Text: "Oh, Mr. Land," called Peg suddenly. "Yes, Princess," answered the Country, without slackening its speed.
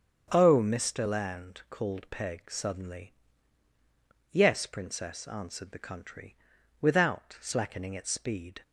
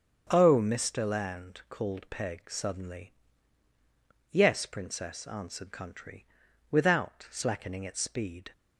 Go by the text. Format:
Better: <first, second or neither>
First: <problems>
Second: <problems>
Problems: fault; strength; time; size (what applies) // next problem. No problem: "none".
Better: first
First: starts louder than the rest; strong; until 1.3 s; 7.5 dB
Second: starts louder than the rest; strong; until 1.3 s; 7 dB // skips "the"; at 5.7 s